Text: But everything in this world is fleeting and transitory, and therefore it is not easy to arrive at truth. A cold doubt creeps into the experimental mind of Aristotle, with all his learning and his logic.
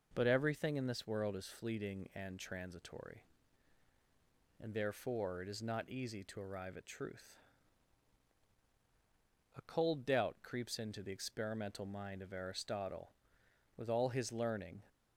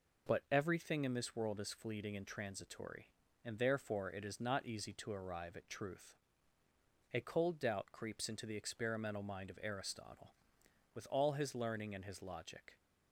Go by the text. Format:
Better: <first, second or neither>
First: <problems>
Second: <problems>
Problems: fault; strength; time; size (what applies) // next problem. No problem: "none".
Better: second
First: stops before "and his logic"; at 14.8 s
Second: none